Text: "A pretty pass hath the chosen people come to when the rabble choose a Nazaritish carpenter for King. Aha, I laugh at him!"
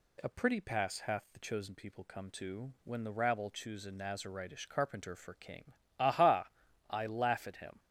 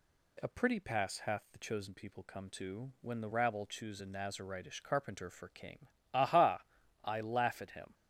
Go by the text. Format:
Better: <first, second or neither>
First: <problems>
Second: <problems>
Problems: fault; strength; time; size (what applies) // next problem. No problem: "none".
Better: neither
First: none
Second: none